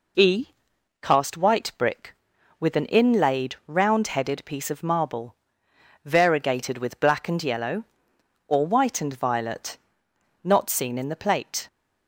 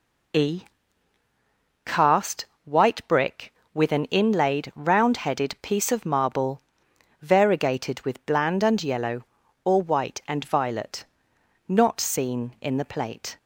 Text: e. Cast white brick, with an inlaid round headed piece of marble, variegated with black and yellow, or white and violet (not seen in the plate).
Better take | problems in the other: first | pauses between "Cast" and "white"; slight; at 2.4 s; 0.18 s long // says "bland" for "black"; at 8.2 s

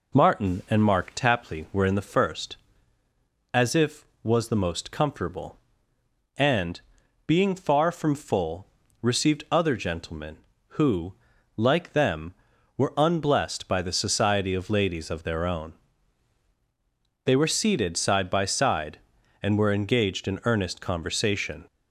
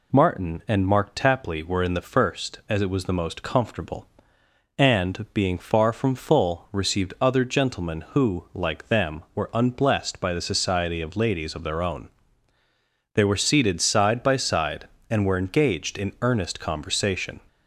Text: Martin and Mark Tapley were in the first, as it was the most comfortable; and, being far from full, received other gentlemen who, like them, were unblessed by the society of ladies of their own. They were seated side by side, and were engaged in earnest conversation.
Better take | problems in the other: second | says "if" for "it"; at 3.7 s

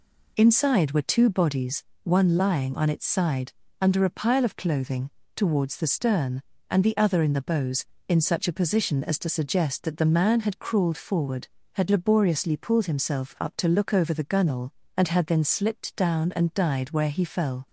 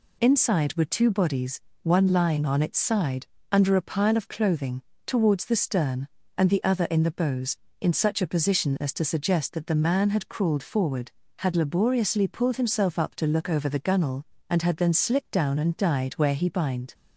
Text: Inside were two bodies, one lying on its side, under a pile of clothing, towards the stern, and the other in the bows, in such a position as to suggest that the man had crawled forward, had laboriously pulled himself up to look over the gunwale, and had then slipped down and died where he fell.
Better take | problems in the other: first | says "bind" for "fell"; at 16.4 s

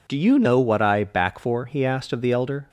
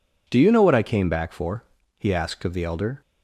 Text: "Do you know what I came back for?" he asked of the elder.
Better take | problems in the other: second | skips "came"; at 1.0 s

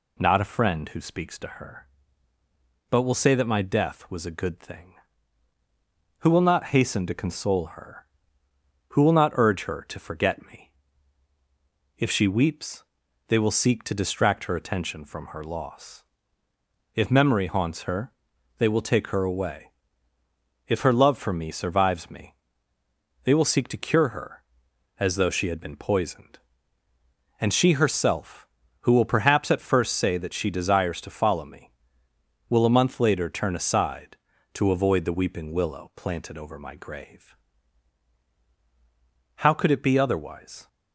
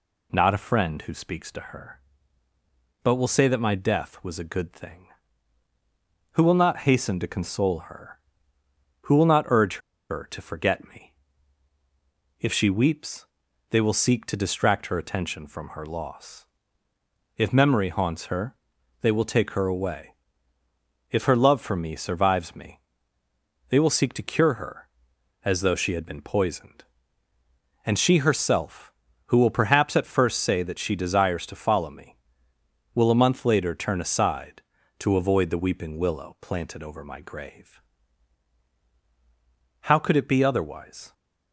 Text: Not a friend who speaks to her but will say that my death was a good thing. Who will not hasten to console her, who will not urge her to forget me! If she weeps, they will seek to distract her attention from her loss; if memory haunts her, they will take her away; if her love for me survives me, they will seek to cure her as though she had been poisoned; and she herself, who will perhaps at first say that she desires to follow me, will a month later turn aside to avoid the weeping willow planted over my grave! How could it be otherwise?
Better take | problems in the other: first | pauses between "urge" and "her"; slight; at 9.7 s; 0.31 s long

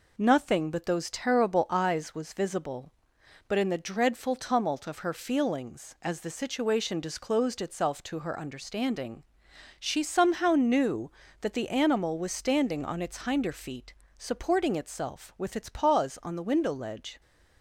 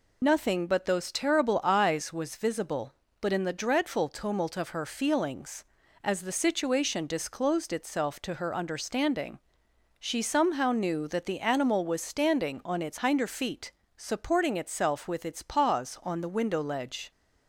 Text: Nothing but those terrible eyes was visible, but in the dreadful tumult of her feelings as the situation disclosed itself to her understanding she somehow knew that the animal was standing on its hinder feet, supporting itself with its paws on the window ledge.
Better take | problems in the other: first | loses the start of "Nothing"; at 0.2 s; 35 ms // pauses between "understanding" and "she"; noticeable; at 9.3 s; 0.60 s long; noticeable in the first

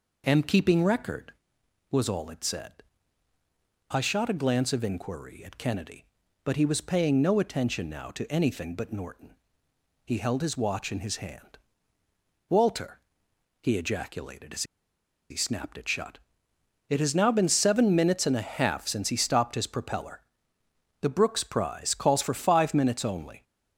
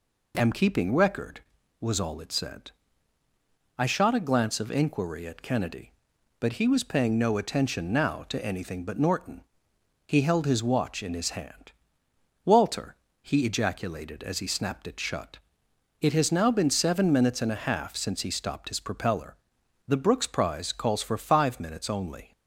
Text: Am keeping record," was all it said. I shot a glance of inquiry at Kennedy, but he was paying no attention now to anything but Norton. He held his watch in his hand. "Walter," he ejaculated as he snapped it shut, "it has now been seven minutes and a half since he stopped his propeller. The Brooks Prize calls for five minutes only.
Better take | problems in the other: second | pauses between "as" and "he"; noticeable; at 14.6 s; 0.67 s long

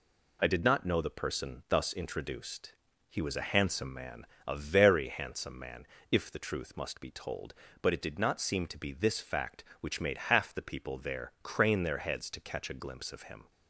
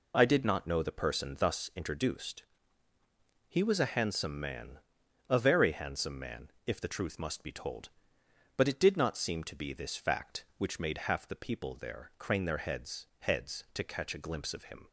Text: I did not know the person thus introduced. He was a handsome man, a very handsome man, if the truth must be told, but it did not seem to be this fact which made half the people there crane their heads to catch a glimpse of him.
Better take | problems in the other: first | says "heads" twice; at 13.1 s

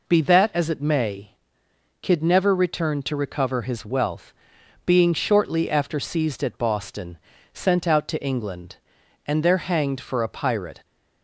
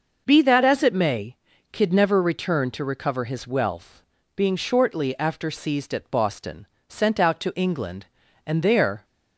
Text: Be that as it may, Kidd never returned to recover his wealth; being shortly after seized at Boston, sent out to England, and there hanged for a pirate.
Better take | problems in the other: first | stops before "hanged for a pirate"; at 9.0 s

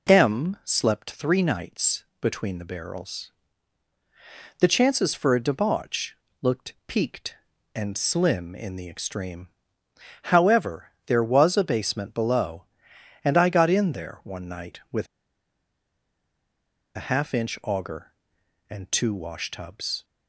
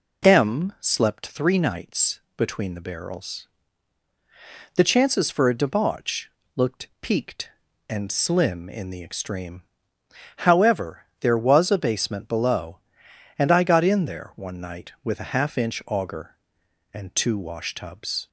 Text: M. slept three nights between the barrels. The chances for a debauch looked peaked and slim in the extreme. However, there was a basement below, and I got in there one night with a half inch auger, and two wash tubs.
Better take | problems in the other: second | pauses between "nights" and "between"; slight; at 2.0 s; 0.18 s long; slight in the second // pauses between "debauch" and "looked"; slight; at 6.1 s; 0.24 s long; slight in the second // pauses between "with" and "a"; strong; at 15.0 s; 1.9 s long

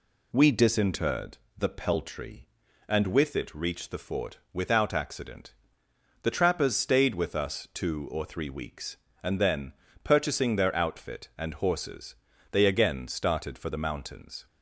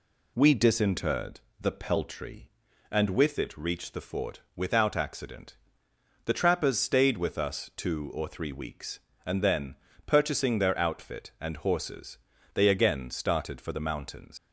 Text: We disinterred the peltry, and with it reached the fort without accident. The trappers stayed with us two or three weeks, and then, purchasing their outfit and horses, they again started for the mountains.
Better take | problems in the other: first | pauses between "disinterred" and "the"; slight; at 1.3 s; 0.22 s long; slight in the first // pauses between "fort" and "without"; slight; at 4.4 s; 0.16 s long; slight in the first // leaves "mountains" unfinished; at 14.3 s; 115 ms

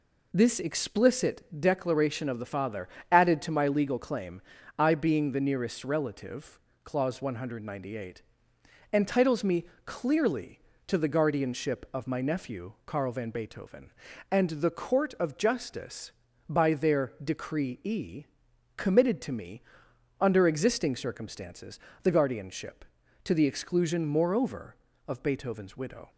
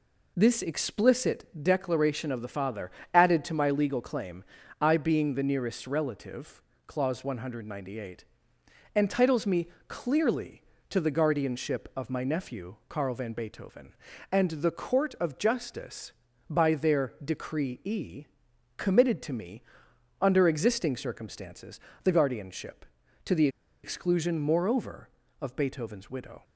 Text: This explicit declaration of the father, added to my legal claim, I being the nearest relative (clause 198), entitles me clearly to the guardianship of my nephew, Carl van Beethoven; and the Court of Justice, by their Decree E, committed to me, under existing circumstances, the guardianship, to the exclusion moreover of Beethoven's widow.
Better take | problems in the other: first | pauses between "me" and "clearly"; slight; at 9.6 s; 0.22 s long; slight in the first // pauses between "the" and "exclusion"; slight; at 23.4 s; 0.35 s long

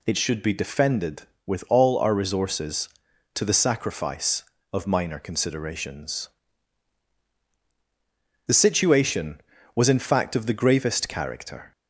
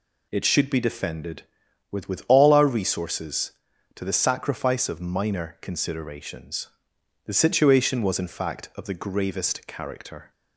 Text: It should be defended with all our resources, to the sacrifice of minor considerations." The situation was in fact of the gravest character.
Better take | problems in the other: first | says "with" twice; at 2.0 s

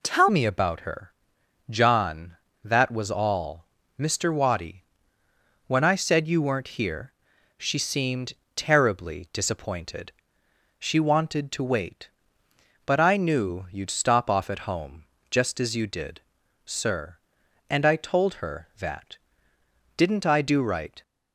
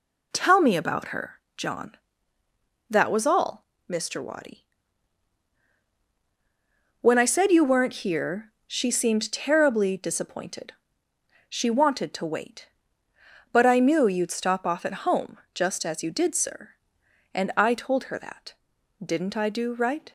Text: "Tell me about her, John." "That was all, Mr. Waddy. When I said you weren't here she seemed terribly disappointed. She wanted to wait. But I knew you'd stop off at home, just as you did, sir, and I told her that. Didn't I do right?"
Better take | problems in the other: second | changes voice at "me"; from 0.2 s on; 20.8 s long // pauses between "here" and "she"; noticeable; at 7.1 s; 0.46 s long; slight in the second // pauses between "seemed" and "terribly"; slight; at 8.3 s; 0.20 s long

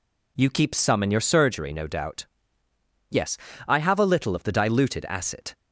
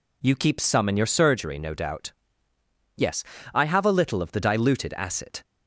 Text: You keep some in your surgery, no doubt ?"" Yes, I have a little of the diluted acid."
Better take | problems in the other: neither | none

